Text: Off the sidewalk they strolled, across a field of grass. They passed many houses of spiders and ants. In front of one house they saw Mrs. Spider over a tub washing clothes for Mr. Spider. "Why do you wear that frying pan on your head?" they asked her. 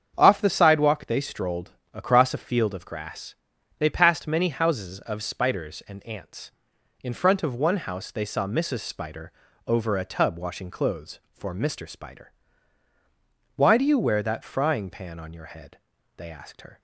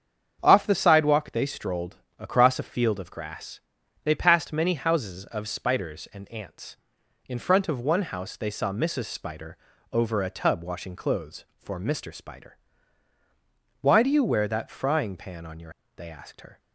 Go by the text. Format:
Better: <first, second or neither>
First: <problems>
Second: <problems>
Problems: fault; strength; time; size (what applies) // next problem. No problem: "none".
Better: first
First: starts louder than the rest; strong; until 1.1 s; 7.5 dB // pauses between "Spider" and "over"; slight; at 9.3 s; 0.34 s long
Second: starts louder than the rest; strong; until 1.4 s; 7.5 dB // pauses between "Spider" and "over"; slight; at 9.5 s; 0.34 s long // skips "head"; at 15.8 s